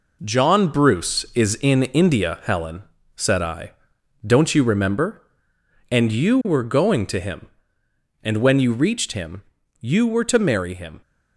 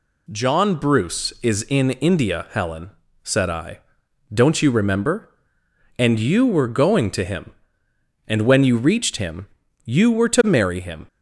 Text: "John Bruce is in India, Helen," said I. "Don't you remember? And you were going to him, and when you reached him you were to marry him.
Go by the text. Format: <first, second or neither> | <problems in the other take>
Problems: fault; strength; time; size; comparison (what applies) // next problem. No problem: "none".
second | gets quieter; throughout; 6.5 dB // pauses between "him" and "you"; at 9.4 s; 0.38 s long; also in the second